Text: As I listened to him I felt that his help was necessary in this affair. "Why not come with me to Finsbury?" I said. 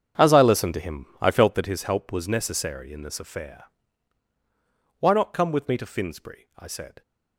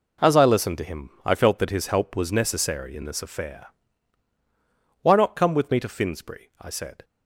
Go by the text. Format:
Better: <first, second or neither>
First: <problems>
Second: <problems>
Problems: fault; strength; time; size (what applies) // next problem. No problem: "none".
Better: second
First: starts louder than the rest; strong; until 1.8 s; 7.5 dB // pauses between "him" and "I"; slight; at 1.0 s; 0.16 s long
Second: pauses between "him" and "I"; slight; at 1.0 s; 0.16 s long